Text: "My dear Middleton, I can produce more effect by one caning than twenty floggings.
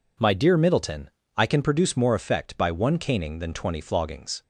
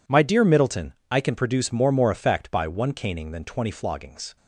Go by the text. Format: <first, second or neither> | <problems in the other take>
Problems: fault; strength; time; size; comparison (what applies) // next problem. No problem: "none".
first | says "more" twice; at 1.8 s